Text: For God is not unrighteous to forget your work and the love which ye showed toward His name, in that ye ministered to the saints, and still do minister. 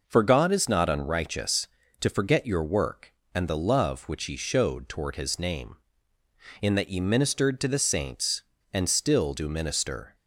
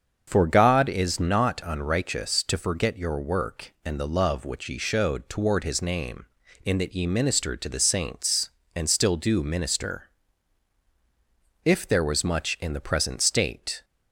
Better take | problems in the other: first | starts louder than the rest; until 1.3 s; 6.5 dB // goes on to say "If there was much in the present state"; strong; from 11.6 s on; 2.2 s long

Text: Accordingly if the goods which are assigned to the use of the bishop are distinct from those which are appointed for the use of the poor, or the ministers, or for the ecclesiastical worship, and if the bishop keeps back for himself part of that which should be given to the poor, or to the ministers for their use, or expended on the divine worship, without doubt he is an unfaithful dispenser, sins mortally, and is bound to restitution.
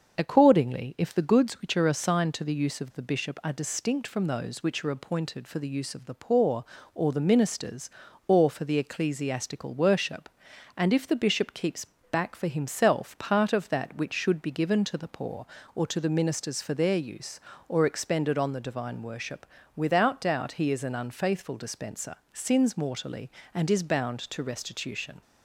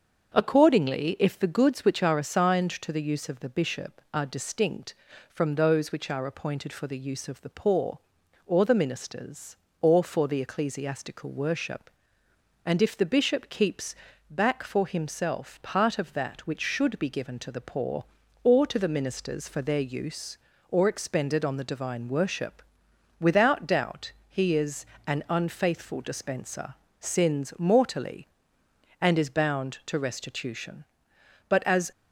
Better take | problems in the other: first | starts louder than the rest; until 1.3 s; 7 dB; also in the first // pauses between "keeps" and "back"; slight; at 13.9 s; 0.36 s long; slight in the first // pauses between "doubt" and "he"; slight; at 24.1 s; 0.16 s long // pauses between "is" and "an"; slight; at 24.8 s; 0.20 s long // goes on to say "But as"; slight; from 31.4 s on; 0.42 s long

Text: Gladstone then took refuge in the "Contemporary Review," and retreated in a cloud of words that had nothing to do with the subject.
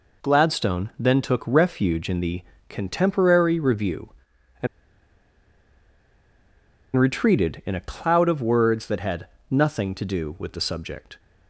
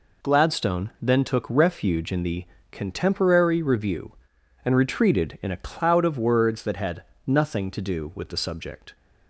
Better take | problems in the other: second | pauses between "the" and "Contemporary"; slight; at 2.4 s; 0.26 s long; slight in the second // pauses between "and" and "retreated"; strong; at 4.6 s; 2.2 s long // pauses between "had" and "nothing"; slight; at 9.2 s; 0.24 s long; slight in the second

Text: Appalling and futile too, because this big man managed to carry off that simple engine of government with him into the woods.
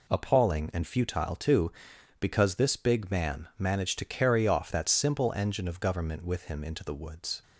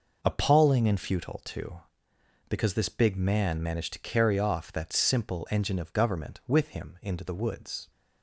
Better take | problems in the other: first | starts louder than the rest; noticeable; until 1.4 s; 5.5 dB

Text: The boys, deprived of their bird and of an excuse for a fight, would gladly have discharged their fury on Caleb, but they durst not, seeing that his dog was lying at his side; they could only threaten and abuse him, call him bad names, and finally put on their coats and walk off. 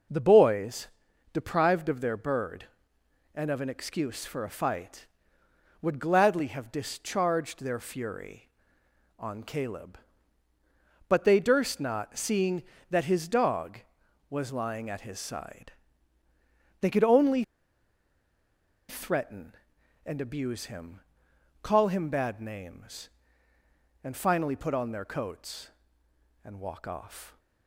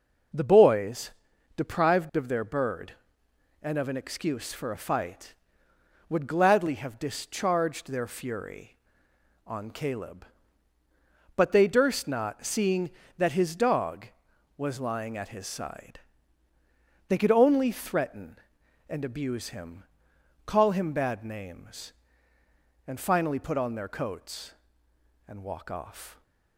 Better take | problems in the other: second | pauses between "only" and "threaten"; strong; at 17.4 s; 1.4 s long

